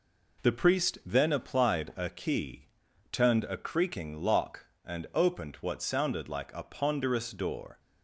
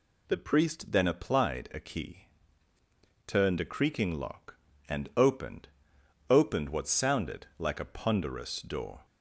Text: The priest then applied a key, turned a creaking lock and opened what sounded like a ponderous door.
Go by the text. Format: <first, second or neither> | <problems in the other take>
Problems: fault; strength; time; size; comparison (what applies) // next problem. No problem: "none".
first | says "opened" twice; at 6.3 s